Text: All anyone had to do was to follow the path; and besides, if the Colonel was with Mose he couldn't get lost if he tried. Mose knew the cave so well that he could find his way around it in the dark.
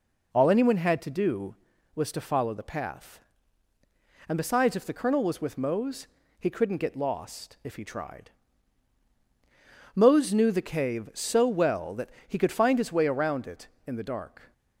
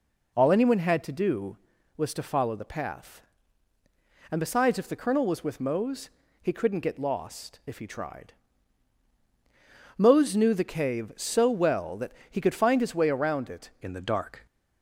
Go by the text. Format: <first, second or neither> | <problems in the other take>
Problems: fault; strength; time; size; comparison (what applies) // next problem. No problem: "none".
first | pauses between "Mose" and "he"; slight; at 6.0 s; 0.32 s long; slight in the first // pauses between "that" and "he"; slight; at 12.1 s; 0.20 s long; slight in the first // changes voice at "in"; from 13.8 s on; 0.6 s long